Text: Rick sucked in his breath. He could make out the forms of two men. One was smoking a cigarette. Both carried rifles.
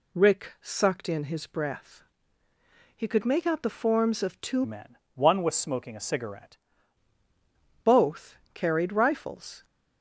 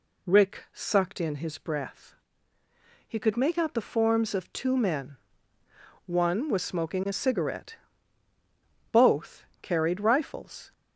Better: second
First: changes voice from "men" to "cigarette"; from 4.6 to 6.5 s; 1.9 s long // pauses between "Both" and "carried"; slight; at 8.3 s; 0.18 s long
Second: pauses between "Both" and "carried"; slight; at 9.4 s; 0.18 s long

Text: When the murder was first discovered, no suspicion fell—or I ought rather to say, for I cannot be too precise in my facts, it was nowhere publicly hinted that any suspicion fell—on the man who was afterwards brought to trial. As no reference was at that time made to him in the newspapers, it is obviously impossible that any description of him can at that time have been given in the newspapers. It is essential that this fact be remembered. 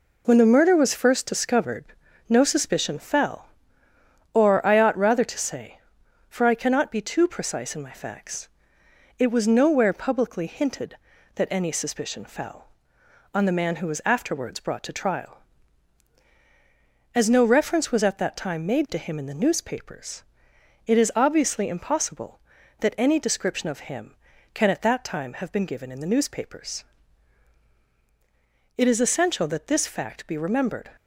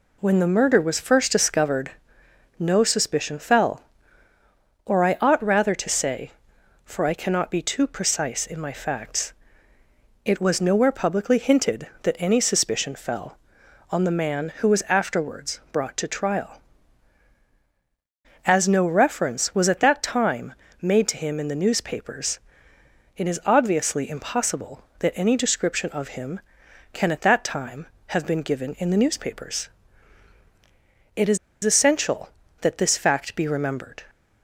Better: first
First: none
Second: pauses between "time" and "made"; slight; at 20.5 s; 0.30 s long // pauses between "is" and "essential"; slight; at 31.3 s; 0.26 s long

